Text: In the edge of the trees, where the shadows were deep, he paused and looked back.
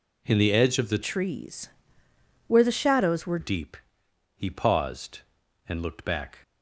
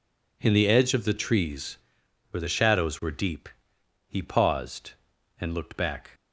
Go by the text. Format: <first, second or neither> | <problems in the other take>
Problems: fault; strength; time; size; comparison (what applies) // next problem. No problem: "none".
second | changes voice from "trees" to "were"; from 1.0 to 3.3 s; 2.3 s long